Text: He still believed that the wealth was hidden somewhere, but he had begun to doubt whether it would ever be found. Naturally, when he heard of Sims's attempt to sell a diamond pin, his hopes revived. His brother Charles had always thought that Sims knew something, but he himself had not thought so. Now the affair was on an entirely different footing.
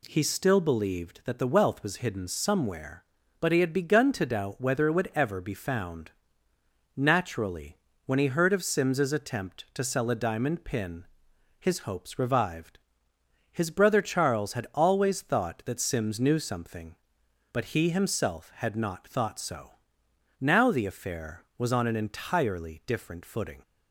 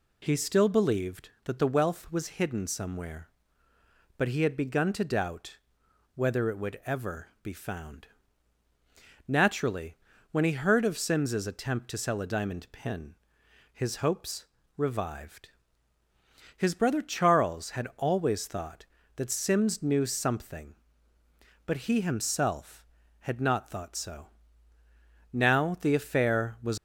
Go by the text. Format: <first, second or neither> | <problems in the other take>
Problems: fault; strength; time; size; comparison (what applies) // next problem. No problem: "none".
first | pauses between "doubt" and "whether"; noticeable; at 5.5 s; 0.58 s long // pauses between "ever" and "be"; slight; at 7.2 s; 0.16 s long // pauses between "hopes" and "revived"; slight; at 14.4 s; 0.32 s long // stops before "on an entirely different footing"; at 26.7 s